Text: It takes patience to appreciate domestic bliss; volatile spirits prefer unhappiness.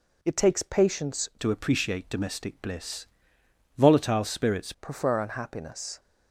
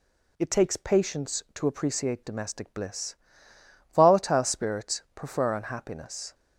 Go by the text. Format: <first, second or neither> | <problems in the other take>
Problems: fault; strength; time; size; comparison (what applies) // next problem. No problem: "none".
second | changes voice from "to" to "spirits"; from 1.3 to 4.7 s; 3.4 s long